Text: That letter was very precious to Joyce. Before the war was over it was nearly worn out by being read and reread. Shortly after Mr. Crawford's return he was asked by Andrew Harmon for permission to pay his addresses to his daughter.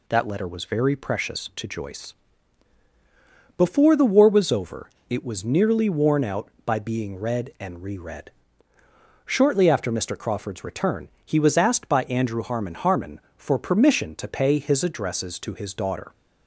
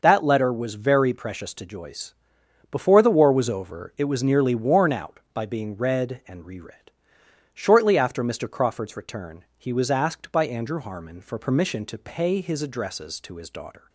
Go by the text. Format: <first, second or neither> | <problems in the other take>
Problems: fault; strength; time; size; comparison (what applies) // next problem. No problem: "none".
second | pauses between "over" and "it"; slight; at 4.9 s; 0.18 s long // pauses between "return" and "he"; slight; at 11.0 s; 0.16 s long // says "Harmon" twice; at 12.7 s